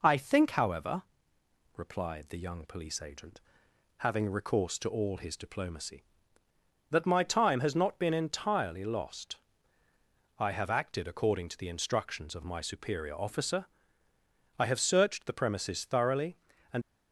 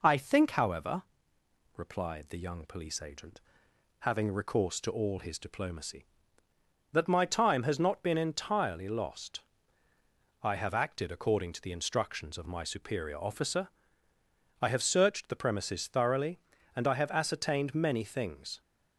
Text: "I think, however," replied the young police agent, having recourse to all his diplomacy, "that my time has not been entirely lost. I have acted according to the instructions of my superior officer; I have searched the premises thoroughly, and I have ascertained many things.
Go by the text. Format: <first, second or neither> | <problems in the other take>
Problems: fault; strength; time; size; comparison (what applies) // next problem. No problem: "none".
second | stops before "I have ascertained many things"; at 16.8 s